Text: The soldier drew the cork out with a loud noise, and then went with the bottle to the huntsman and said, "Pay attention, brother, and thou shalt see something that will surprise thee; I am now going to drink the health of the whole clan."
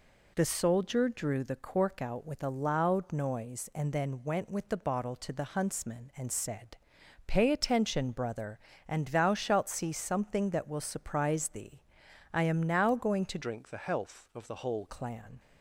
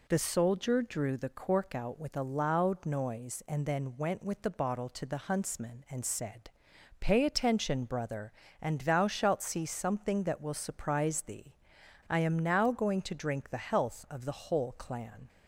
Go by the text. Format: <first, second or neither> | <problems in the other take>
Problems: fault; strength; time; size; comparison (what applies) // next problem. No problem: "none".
second | changes voice from "drink" to "whole"; from 13.4 to 14.8 s; 1.4 s long